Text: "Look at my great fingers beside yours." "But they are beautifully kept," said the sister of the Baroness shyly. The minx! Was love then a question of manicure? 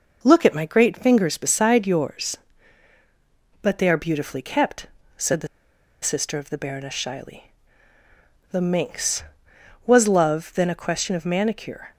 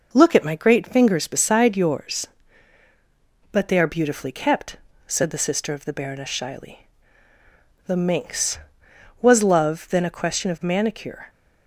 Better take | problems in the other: second | pauses between "the" and "sister"; noticeable; at 5.4 s; 0.56 s long

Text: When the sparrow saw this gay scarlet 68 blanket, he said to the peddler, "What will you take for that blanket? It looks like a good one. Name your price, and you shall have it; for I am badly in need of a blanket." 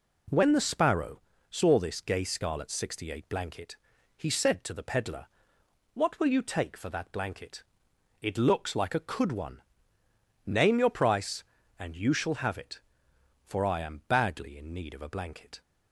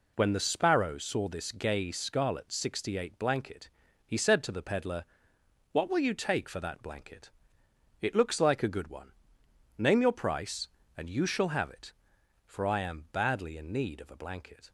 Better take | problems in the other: second | pauses between "sparrow" and "saw"; slight; at 1.2 s; 0.28 s long // says "could" for "good"; at 8.9 s

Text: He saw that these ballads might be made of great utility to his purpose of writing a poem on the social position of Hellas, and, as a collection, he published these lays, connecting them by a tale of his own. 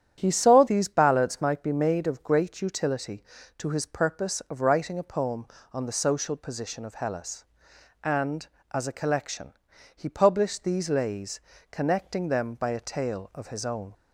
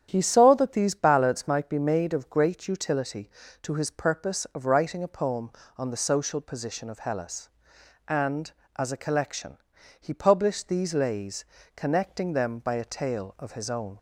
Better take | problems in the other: second | starts louder than the rest; strong; until 1.2 s; 10 dB; strong in the second // skips "that"; at 0.6 s

